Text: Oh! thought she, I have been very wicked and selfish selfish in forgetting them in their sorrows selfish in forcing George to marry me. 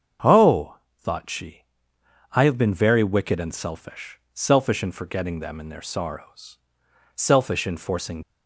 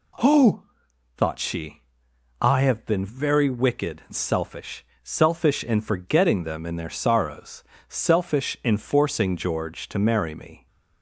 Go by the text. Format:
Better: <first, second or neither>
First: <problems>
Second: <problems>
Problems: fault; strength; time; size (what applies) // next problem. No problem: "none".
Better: second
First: starts louder than the rest; until 1.4 s; 7 dB // pauses between "selfish" and "selfish"; slight; at 4.1 s; 0.16 s long // pauses between "sorrows" and "selfish"; noticeable; at 6.5 s; 0.56 s long // stops before "George to marry me"; at 8.2 s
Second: pauses between "selfish" and "selfish"; slight; at 4.8 s; 0.22 s long // pauses between "sorrows" and "selfish"; slight; at 7.6 s; 0.26 s long